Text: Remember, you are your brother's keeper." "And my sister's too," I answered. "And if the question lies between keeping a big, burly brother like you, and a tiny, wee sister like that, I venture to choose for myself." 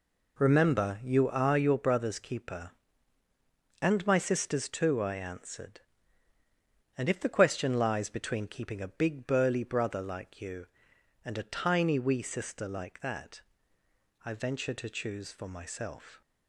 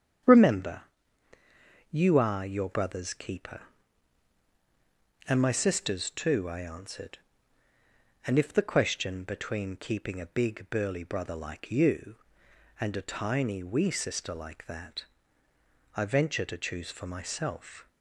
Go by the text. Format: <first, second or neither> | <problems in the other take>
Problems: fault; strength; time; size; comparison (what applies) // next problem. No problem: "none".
first | starts louder than the rest; strong; until 2.3 s; 8.5 dB // skips "lies"; at 9.2 s